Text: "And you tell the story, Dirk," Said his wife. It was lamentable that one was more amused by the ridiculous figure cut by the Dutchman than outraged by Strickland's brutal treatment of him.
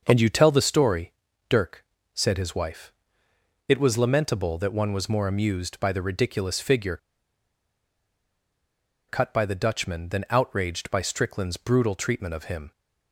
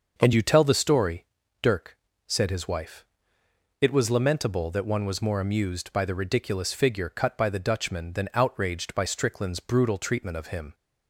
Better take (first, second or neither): second